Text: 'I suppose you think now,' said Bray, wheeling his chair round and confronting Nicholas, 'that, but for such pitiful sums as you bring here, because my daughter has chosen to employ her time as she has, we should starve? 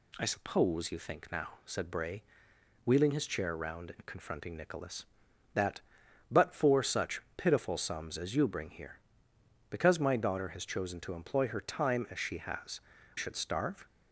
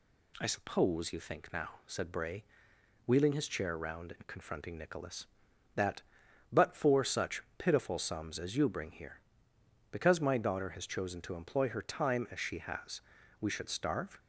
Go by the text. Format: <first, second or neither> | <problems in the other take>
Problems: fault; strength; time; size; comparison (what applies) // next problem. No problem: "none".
second | skips "we"; at 12.9 s